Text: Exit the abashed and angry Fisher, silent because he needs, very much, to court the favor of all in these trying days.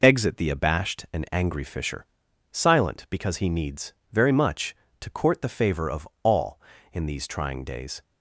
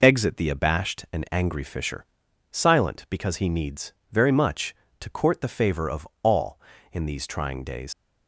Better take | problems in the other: first | pauses between "of" and "all"; slight; at 6.0 s; 0.16 s long; slight in the first // leaves "days" unfinished; at 7.9 s; 90 ms

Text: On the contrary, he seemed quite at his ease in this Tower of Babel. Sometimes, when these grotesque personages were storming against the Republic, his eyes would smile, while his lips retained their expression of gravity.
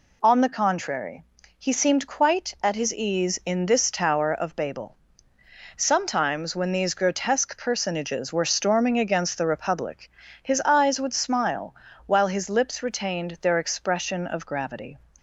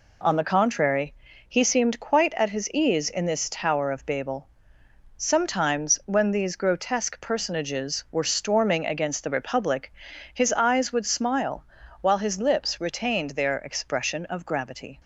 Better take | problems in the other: neither | none

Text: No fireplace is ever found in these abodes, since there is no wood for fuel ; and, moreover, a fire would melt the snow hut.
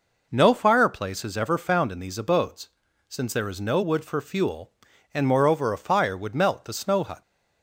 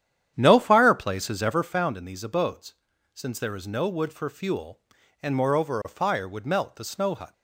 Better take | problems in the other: first | starts louder than the rest; strong; until 1.7 s; 9.5 dB

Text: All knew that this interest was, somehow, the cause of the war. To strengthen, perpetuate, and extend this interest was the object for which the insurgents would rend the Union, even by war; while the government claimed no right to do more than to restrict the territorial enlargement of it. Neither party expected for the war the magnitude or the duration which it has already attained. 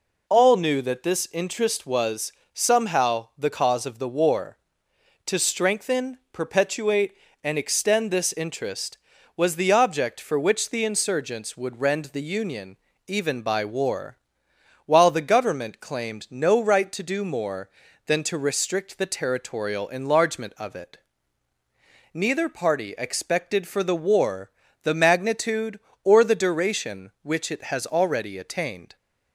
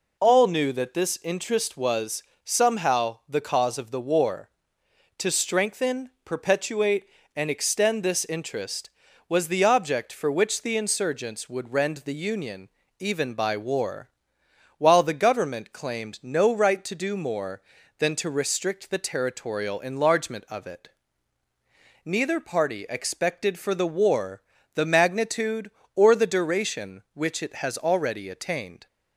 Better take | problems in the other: neither | pauses between "war" and "the"; slight; the same in both

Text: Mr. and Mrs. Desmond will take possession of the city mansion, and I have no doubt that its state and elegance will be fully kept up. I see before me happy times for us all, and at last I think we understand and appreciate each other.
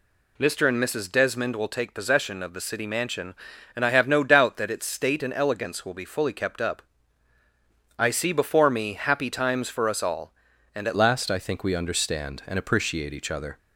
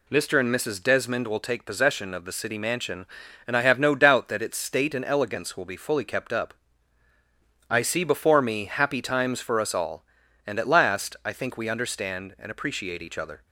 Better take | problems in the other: second | changes voice at "last"; from 10.9 s on; 2.6 s long

